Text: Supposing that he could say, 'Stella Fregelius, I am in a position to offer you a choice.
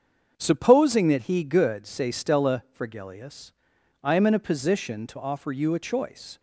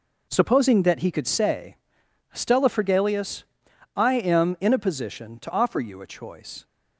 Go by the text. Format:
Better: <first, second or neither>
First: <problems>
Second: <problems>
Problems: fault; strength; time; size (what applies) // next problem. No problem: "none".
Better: second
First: starts louder than the rest; until 1.3 s; 7 dB // says "good" for "could"; at 1.4 s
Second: none